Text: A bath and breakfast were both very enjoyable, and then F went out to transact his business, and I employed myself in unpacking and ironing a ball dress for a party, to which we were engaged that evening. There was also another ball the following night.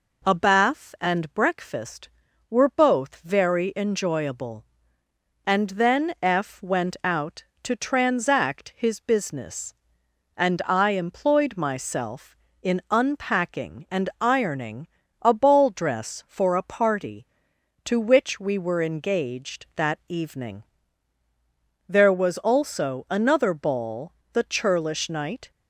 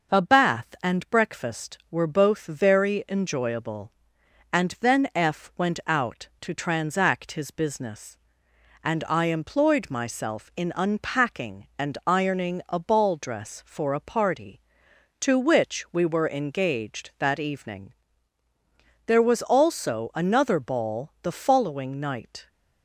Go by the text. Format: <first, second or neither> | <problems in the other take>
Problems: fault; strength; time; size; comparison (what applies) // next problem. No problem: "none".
second | pauses between "ironing" and "a"; slight; at 14.8 s; 0.36 s long // pauses between "ball" and "the"; slight; at 24.1 s; 0.22 s long // says "churlish" for "following"; at 24.4 s